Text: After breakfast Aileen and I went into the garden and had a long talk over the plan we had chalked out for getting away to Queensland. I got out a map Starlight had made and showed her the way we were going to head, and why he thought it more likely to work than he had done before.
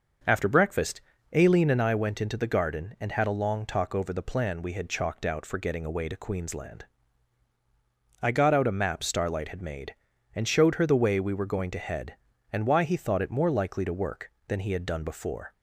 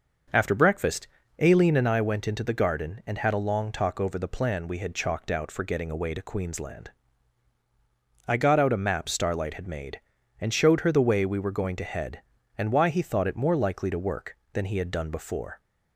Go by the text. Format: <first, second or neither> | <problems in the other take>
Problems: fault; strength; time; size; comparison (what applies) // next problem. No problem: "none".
neither | starts louder than the rest; the same in both // pauses between "breakfast" and "Aileen"; slight; the same in both